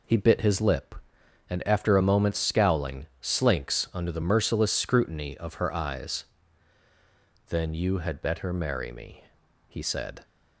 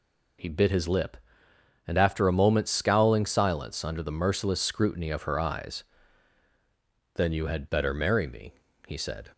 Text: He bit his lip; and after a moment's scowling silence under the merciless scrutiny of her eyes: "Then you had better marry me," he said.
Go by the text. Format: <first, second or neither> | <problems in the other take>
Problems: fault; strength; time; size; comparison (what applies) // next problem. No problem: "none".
second | says "slinks" for "silence"; at 3.2 s